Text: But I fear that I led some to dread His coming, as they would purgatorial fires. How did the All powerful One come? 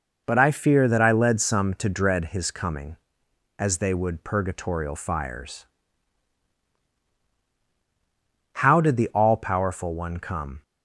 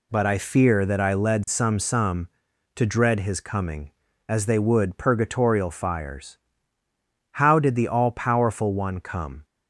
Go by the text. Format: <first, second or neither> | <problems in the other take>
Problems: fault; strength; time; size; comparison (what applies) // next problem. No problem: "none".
first | says "some" twice; at 1.7 s